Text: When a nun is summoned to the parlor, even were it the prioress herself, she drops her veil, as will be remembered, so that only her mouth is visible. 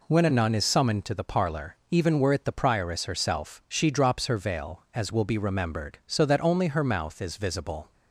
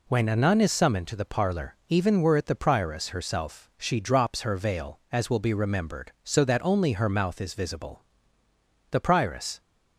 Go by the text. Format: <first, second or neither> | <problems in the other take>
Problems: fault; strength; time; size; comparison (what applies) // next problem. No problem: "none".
first | goes on to say "The prioress"; noticeable; from 8.9 s on; 0.68 s long